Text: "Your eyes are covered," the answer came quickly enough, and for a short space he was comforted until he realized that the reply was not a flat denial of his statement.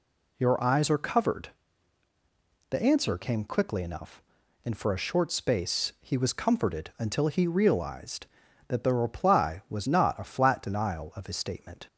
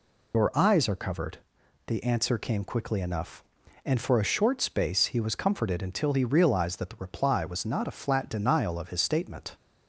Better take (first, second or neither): first